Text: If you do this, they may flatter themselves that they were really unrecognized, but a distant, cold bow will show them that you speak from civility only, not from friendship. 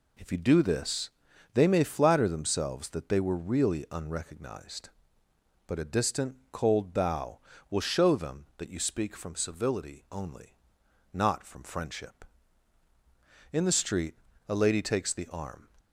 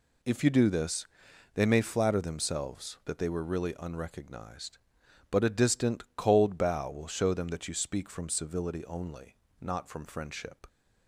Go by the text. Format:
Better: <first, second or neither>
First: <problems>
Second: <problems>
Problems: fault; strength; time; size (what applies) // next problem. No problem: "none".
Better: second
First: goes on to say "In the street a lady takes the arm"; strong; from 13.5 s on; 2.1 s long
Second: none